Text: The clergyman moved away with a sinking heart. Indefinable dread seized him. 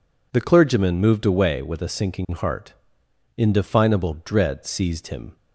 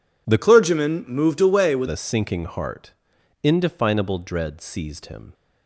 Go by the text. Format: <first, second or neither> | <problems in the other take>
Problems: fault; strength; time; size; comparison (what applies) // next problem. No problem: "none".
first | changes voice from "clergyman" to "with"; from 0.4 to 1.8 s; 1.4 s long